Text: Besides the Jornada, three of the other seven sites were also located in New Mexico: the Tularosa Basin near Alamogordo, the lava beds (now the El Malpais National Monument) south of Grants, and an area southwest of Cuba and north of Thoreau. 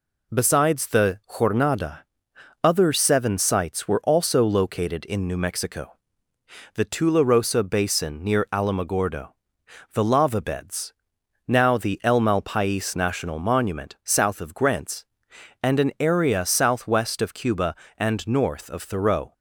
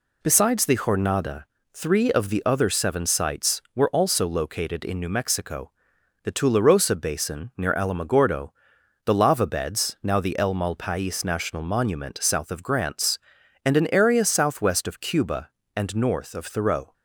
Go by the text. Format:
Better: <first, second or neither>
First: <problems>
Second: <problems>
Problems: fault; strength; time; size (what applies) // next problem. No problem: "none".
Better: second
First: skips "three of the"; at 2.3 s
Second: none